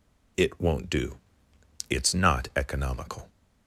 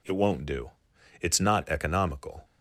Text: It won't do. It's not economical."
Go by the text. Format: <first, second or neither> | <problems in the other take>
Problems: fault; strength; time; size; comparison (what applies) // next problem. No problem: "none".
neither | none